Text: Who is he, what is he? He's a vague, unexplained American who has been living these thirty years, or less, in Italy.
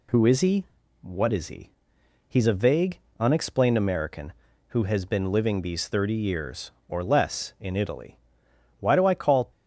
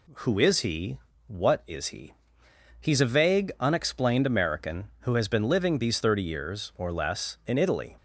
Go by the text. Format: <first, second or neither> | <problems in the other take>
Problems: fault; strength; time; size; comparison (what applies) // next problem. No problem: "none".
second | goes on to say "Why do I call"; noticeable; from 8.8 s on; 0.70 s long